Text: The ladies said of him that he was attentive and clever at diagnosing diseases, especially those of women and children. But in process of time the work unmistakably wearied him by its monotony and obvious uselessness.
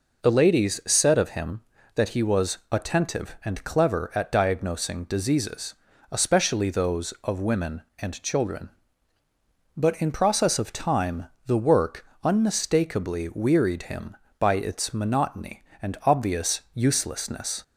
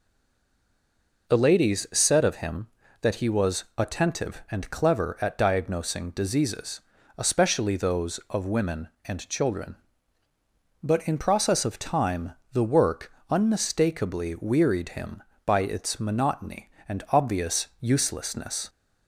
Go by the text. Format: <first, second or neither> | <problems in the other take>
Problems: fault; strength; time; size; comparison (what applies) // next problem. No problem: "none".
first | stays silent before the first word; noticeable; until 1.2 s; 1.2 s long // pauses between "time" and "the"; slight; at 12.3 s; 0.20 s long; slight in the first // pauses between "work" and "unmistakably"; slight; at 13.1 s; 0.18 s long; slight in the first